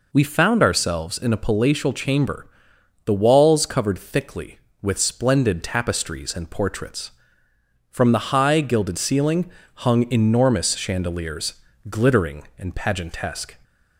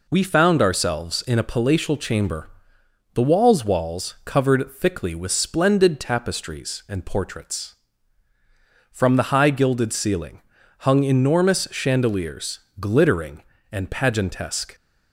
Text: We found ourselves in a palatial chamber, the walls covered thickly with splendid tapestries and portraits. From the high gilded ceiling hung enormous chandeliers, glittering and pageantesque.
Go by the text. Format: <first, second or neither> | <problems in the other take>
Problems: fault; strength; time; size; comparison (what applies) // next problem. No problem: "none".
first | says "walls" twice; at 3.6 s // pauses between "ceiling" and "hung"; at 10.4 s; 0.37 s long; slight in the first